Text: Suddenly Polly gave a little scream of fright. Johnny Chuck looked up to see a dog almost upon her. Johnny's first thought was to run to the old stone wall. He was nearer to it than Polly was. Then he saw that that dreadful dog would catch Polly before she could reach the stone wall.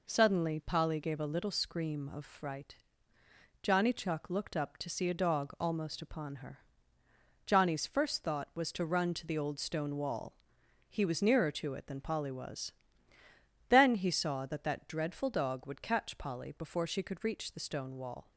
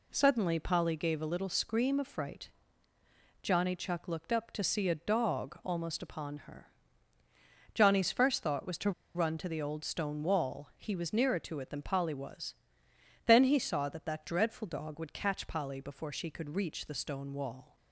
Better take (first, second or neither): first